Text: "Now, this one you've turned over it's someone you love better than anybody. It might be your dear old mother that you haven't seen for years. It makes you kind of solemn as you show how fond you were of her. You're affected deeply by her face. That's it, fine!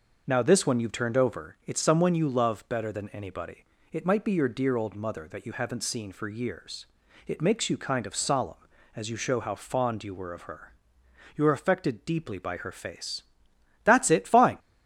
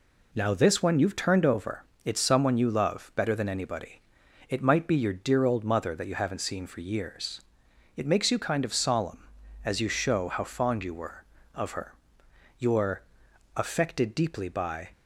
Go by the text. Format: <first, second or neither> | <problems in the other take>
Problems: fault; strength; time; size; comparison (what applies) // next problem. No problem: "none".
first | pauses between "over" and "it's"; slight; at 1.8 s; 0.20 s long // pauses between "You're" and "affected"; noticeable; at 13.0 s; 0.54 s long // stops before "her face That's it fine"; at 14.9 s